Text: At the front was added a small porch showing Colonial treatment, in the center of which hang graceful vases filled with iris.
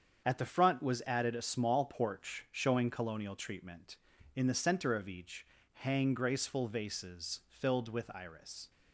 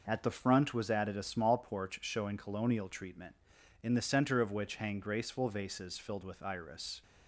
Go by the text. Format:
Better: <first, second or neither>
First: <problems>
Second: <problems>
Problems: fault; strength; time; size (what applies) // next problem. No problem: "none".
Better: second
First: starts louder than the rest; strong; until 1.2 s; 7.5 dB // says "each" for "which"; at 5.0 s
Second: none